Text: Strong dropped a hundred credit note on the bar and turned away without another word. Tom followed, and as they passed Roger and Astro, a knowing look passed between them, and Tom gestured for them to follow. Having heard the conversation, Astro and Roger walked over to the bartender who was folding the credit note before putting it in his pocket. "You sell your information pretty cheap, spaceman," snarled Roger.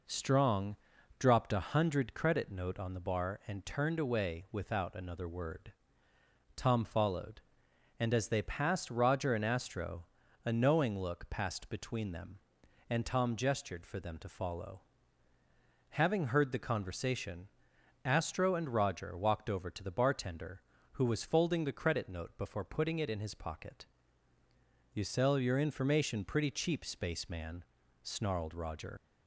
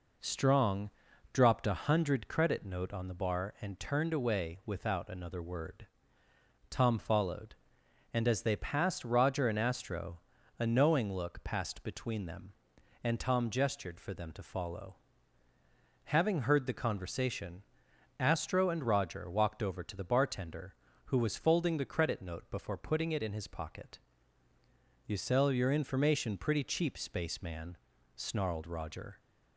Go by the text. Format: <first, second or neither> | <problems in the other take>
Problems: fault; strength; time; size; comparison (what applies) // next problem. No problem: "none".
second | pauses between "Strong" and "dropped"; at 0.7 s; 0.42 s long; also in the second // leaves "Roger" unfinished; at 28.9 s; 85 ms